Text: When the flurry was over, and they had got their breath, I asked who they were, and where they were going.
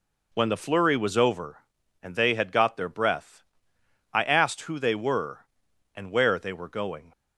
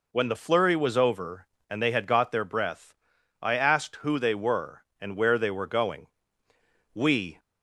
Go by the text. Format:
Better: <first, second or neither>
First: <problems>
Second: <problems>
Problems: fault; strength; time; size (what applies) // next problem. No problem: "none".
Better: first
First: none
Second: goes on to say "We"; slight; from 6.9 s on; 0.46 s long